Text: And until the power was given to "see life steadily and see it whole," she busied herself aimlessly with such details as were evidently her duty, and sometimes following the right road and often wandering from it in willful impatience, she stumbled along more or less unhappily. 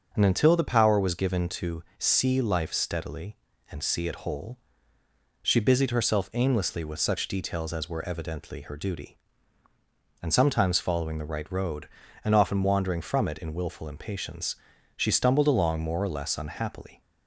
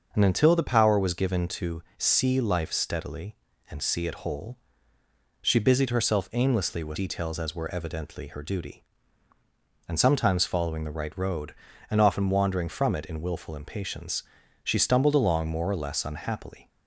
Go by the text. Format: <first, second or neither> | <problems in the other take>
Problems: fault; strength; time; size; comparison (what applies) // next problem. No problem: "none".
first | starts louder than the rest; until 1.1 s; 6 dB; also in the first // skips "such"; at 6.9 s